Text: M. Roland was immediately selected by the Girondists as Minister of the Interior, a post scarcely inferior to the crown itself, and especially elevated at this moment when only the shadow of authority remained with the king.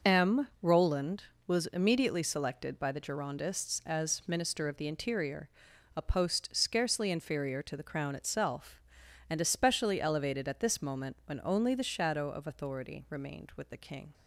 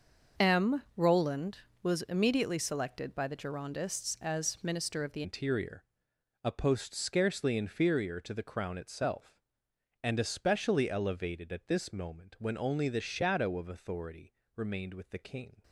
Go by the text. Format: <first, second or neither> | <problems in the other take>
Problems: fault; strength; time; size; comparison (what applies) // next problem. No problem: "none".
first | starts louder than the rest; until 1.5 s; 6 dB; noticeable in the first // changes voice at "Interior"; from 5.2 s on; 10.4 s long // pauses between "authority" and "remained"; slight; at 14.3 s; 0.24 s long